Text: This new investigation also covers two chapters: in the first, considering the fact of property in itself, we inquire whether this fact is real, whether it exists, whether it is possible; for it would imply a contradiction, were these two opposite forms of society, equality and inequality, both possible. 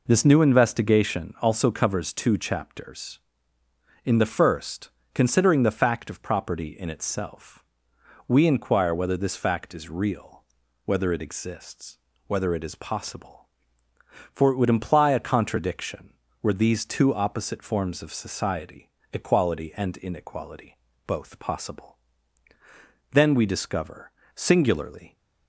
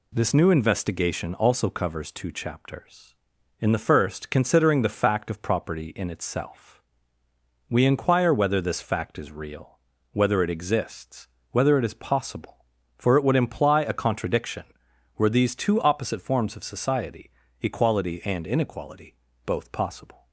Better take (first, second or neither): second